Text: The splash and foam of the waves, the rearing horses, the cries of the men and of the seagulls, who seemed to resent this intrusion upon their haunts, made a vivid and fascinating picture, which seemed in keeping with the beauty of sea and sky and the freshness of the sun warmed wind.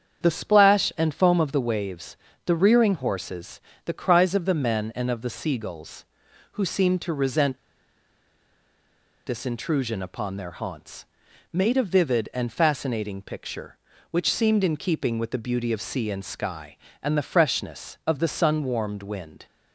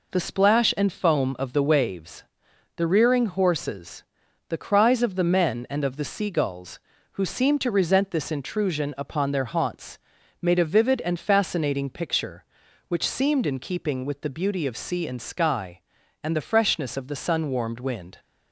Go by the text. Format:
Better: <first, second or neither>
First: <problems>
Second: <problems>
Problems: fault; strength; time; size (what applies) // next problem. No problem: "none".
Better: second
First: starts louder than the rest; strong; until 1.2 s; 8 dB // pauses between "resent" and "this"; strong; at 7.5 s; 1.6 s long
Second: none